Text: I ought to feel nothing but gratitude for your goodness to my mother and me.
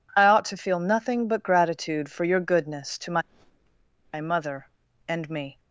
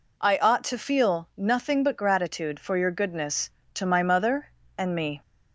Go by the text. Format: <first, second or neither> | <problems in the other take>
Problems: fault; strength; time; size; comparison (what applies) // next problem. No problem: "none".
second | says "my" twice; at 4.1 s